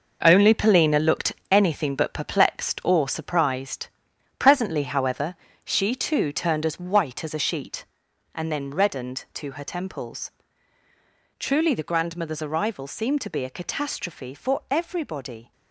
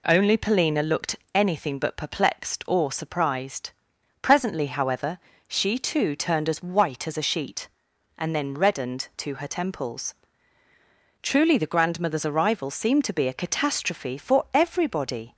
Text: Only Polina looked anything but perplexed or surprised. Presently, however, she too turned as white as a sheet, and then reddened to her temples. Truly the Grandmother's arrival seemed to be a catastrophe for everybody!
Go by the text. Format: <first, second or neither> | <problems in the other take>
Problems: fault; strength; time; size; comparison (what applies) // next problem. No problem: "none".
second | gets quieter; strong; throughout; 9 dB // pauses between "looked" and "anything"; slight; at 1.3 s; 0.18 s long; slight in the second